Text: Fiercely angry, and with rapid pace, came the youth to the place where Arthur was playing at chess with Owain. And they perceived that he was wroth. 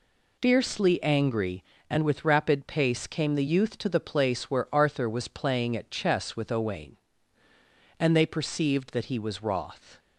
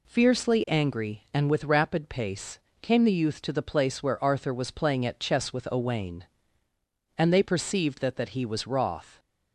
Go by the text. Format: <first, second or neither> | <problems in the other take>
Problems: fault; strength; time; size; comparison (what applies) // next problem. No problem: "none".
first | says "that" twice; at 8.1 s